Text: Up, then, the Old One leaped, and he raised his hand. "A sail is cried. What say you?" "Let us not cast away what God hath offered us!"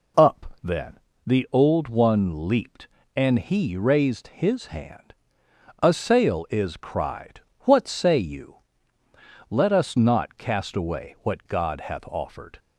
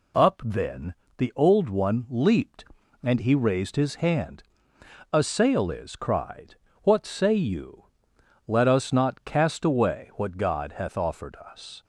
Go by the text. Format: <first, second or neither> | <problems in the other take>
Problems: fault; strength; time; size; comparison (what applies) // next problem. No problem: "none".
second | stops before "us"; at 12.5 s